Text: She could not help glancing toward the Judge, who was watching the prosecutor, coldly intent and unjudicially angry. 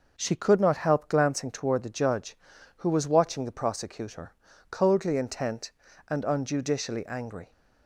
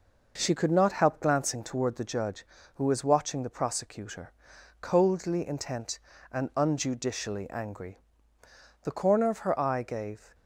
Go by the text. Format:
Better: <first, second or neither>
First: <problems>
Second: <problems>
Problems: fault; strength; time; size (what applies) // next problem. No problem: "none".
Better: first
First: none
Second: goes on to say "The corner of her eye gave"; from 8.8 s on; 1.5 s long